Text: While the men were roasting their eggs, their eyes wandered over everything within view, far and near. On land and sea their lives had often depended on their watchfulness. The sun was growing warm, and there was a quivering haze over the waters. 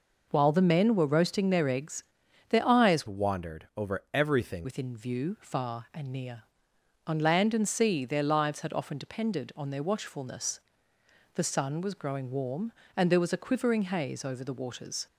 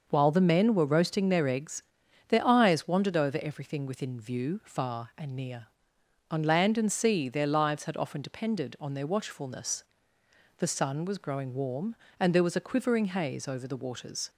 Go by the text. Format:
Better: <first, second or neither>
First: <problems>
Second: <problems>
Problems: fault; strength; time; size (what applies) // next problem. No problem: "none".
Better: second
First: changes voice from "wandered" to "everything"; from 3.0 to 4.6 s; 1.6 s long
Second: none